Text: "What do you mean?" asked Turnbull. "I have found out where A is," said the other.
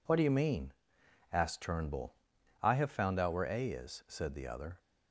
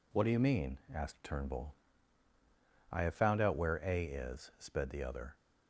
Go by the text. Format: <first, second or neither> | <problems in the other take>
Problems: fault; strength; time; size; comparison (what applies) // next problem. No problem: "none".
first | says "sped" for "said"; at 4.5 s